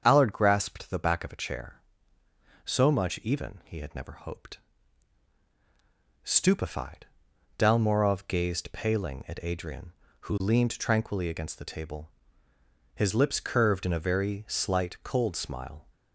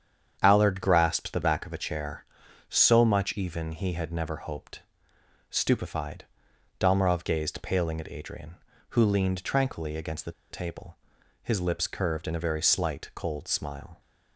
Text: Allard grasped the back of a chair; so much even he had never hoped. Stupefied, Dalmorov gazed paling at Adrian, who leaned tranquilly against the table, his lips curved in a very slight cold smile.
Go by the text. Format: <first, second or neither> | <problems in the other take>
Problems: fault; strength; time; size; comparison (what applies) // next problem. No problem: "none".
first | starts louder than the rest; strong; until 1.4 s; 8 dB; strong in the first // pauses between "the" and "table"; slight; at 10.3 s; 0.20 s long